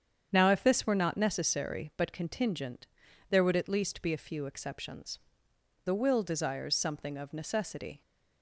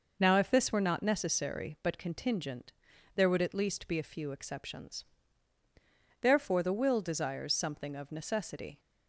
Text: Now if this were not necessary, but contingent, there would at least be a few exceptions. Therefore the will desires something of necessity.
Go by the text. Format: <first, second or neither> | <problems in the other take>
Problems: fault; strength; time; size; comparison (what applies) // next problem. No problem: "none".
second | starts louder than the rest; strong; until 1.3 s; 8 dB // skips "Therefore"; at 5.5 s